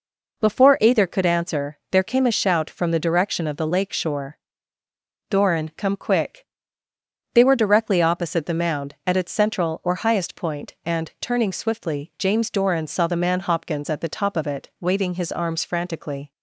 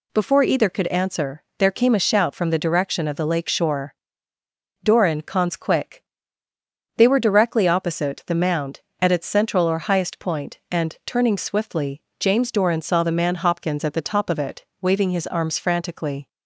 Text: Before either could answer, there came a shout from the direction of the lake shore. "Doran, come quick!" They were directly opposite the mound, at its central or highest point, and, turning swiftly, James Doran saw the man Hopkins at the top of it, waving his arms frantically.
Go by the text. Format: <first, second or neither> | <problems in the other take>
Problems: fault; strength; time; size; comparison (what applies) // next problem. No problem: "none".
first | says "cons" for "come"; at 5.2 s